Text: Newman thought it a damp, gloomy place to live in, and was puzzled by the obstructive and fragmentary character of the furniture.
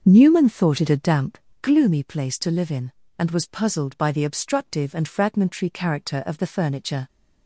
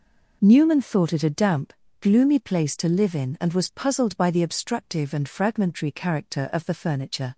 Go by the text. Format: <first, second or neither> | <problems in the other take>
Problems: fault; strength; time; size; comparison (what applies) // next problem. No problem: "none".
second | starts louder than the rest; until 1.7 s; 6.5 dB